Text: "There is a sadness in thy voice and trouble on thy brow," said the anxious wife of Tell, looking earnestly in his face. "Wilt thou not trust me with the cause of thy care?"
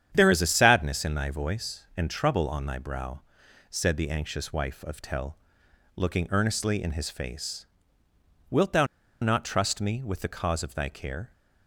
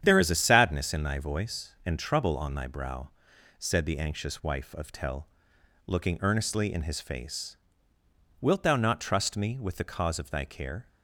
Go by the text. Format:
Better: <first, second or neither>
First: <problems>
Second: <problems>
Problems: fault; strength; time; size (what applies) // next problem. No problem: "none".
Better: second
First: starts louder than the rest; strong; until 1.1 s; 9 dB // pauses between "thou" and "not"; at 8.8 s; 0.36 s long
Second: starts louder than the rest; strong; until 1.0 s; 9 dB